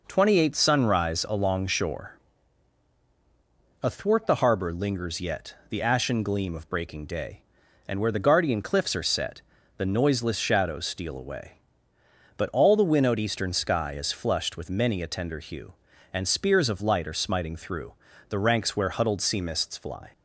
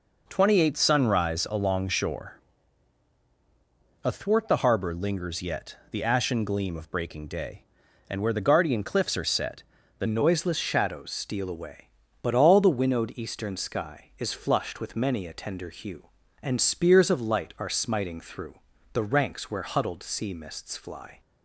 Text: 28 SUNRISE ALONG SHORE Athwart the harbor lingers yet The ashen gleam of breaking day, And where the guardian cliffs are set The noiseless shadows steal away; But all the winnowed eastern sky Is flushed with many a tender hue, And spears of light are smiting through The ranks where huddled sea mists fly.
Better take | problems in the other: first | pauses between "SHORE" and "Athwart"; strong; at 2.4 s; 1.6 s long; strong in the first // pauses between "set" and "The"; slight; at 9.6 s; 0.34 s long; slight in the first // changes voice at "noiseless"; from 10.0 s on; 11.1 s long // pauses between "through" and "The"; slight; at 18.5 s; 0.36 s long; slight in the first

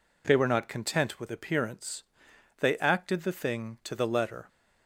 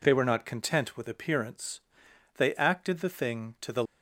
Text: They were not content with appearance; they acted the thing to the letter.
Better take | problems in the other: first | stops before "letter"; at 3.8 s

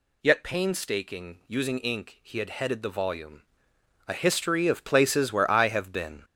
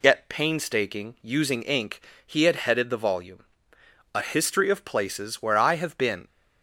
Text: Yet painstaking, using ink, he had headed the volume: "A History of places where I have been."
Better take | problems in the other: second | gets louder; noticeable; throughout; 6 dB

